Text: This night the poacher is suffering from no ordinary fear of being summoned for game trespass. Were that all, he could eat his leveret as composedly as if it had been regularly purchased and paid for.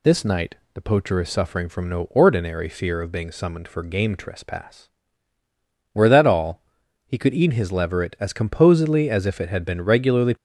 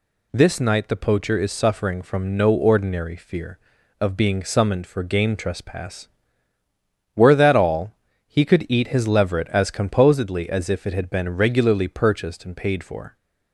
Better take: second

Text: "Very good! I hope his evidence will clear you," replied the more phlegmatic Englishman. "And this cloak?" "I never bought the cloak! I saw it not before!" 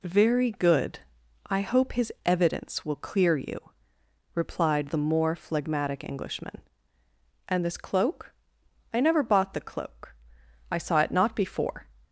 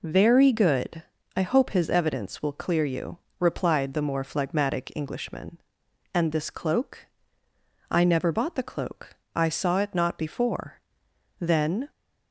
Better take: first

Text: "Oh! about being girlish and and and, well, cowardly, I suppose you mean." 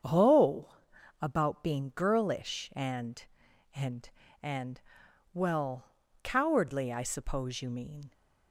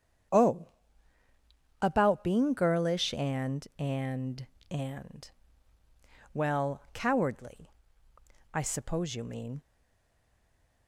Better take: first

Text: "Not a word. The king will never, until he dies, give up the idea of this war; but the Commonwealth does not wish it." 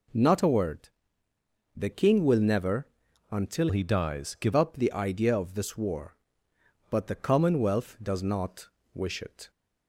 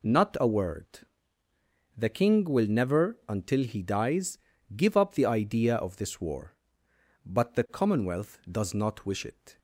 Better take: second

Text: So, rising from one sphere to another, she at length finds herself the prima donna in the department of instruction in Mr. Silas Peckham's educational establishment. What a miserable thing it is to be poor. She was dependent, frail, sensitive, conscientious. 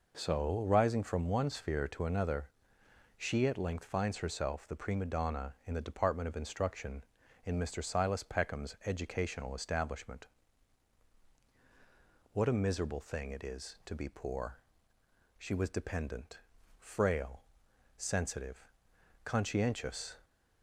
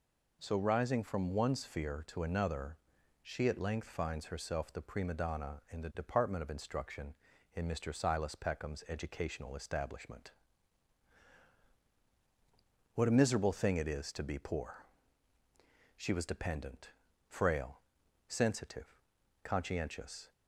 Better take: neither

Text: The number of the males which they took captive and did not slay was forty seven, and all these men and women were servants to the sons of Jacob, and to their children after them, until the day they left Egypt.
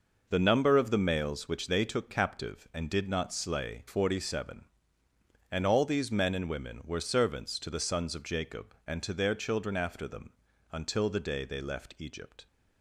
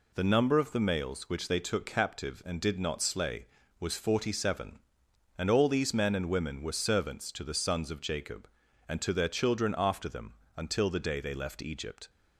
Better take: second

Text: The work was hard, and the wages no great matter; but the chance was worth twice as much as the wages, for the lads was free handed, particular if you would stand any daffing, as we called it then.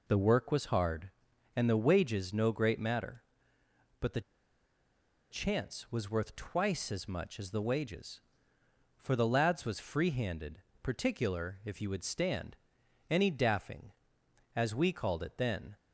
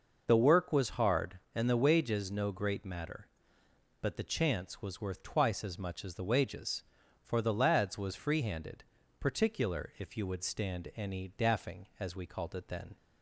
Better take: second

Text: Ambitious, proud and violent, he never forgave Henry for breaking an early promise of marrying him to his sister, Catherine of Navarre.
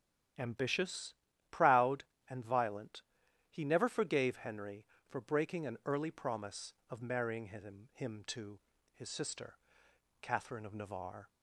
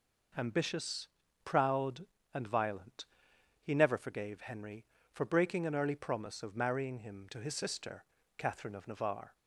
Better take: second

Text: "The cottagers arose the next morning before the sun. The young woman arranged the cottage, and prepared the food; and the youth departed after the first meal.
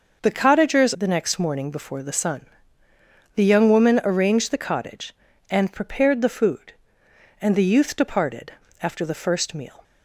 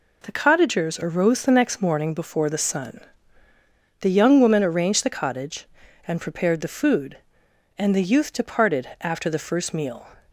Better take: second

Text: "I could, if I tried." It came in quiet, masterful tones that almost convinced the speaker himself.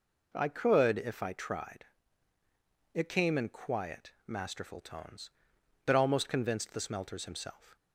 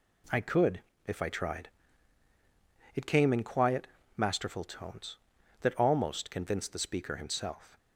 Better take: second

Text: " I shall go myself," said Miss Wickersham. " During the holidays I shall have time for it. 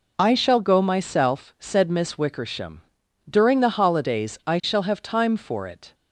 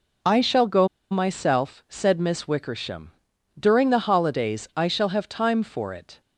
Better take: first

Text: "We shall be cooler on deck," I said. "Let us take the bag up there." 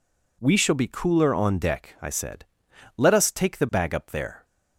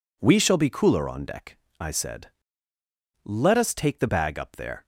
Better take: neither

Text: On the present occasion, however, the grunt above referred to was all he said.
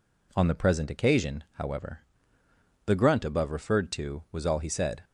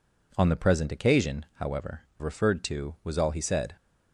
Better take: first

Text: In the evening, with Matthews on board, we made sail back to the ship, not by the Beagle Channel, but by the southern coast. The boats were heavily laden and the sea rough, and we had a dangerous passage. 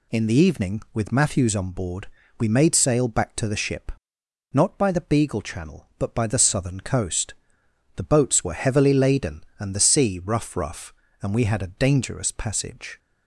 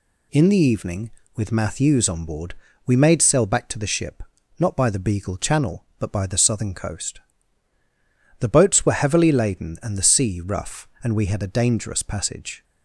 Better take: second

